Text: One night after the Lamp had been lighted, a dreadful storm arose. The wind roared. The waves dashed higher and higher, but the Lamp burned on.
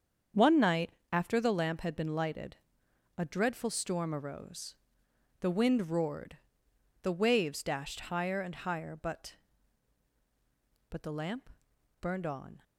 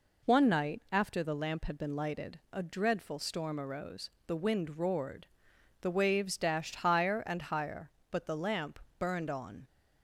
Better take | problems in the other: second | starts louder than the rest; strong; until 1.5 s; 7.5 dB // pauses between "night" and "after"; slight; at 0.9 s; 0.22 s long // says "but" twice; at 10.8 s // pauses between "Lamp" and "burned"; noticeable; at 11.4 s; 0.52 s long; slight in the second

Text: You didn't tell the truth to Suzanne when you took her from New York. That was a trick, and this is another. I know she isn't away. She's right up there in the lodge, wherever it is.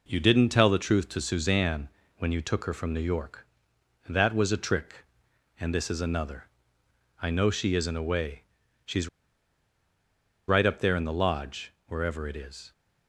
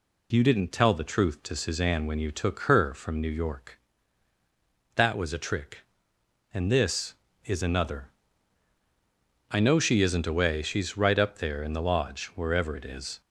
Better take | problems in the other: second | pauses between "Suzanne" and "when"; slight; at 1.8 s; 0.30 s long // pauses between "She's" and "right"; strong; at 9.0 s; 1.3 s long

